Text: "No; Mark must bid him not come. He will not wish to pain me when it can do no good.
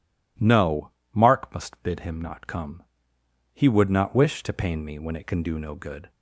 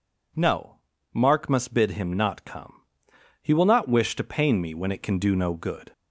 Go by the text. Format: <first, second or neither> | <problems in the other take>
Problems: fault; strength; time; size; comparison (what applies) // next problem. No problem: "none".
second | says "would" for "will"; at 3.6 s